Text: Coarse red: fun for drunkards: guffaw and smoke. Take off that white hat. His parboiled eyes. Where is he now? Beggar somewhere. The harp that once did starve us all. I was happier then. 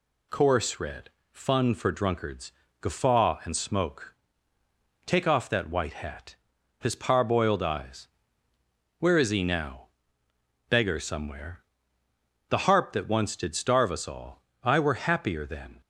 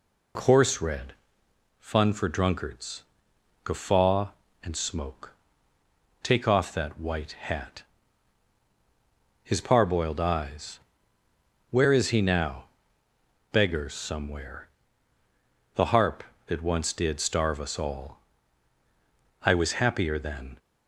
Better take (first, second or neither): second